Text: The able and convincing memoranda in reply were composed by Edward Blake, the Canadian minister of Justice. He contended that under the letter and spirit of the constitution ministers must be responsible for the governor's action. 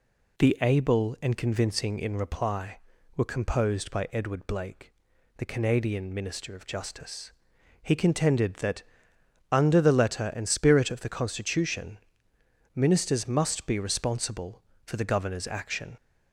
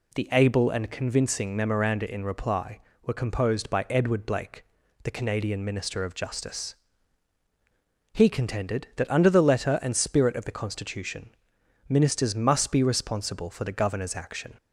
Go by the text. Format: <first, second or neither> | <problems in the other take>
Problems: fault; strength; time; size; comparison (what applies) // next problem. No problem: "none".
second | skips "memoranda"; at 1.9 s // pauses between "that" and "under"; noticeable; at 8.8 s; 0.68 s long // pauses between "constitution" and "ministers"; noticeable; at 11.9 s; 0.78 s long; noticeable in the second